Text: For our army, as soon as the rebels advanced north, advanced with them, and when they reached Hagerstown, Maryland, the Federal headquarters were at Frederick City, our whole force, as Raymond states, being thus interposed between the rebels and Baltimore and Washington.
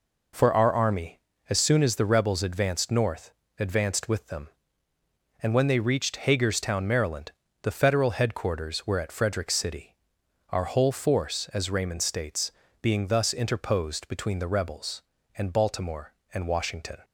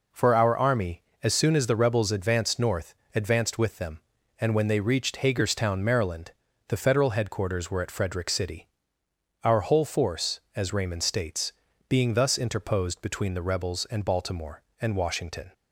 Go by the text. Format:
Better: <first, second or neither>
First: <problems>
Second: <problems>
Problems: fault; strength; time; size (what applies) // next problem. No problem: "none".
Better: neither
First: none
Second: none